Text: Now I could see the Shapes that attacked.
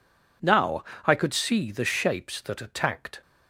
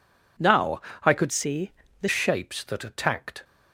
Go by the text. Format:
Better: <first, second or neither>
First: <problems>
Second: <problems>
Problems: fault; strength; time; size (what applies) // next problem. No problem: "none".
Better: first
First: pauses between "Now" and "I"; slight; at 0.8 s; 0.18 s long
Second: pauses between "Now" and "I"; slight; at 0.8 s; 0.20 s long // changes voice from "see" to "the"; from 1.3 to 2.0 s; 0.7 s long // pauses between "see" and "the"; slight; at 1.7 s; 0.30 s long